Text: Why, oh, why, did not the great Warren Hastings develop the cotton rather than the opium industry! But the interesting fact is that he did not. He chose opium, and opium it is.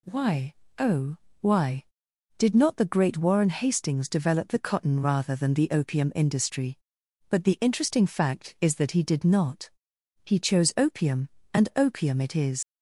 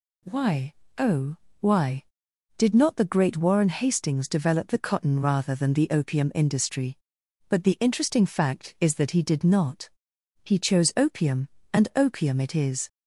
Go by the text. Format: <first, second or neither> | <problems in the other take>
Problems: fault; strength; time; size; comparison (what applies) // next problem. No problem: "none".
second | leaves "is" unfinished; at 12.6 s; 55 ms